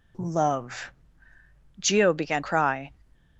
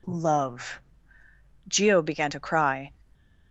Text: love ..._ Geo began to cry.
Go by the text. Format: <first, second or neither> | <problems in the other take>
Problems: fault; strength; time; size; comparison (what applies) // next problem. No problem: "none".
second | skips "to"; at 2.4 s